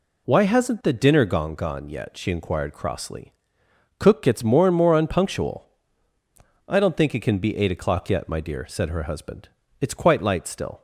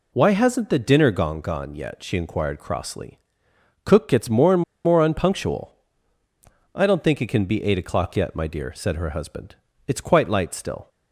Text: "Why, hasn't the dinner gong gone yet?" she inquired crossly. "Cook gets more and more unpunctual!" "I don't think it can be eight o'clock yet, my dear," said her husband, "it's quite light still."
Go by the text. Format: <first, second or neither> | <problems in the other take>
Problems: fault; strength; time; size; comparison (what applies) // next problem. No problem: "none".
first | pauses between "and" and "more"; slight; at 4.6 s; 0.23 s long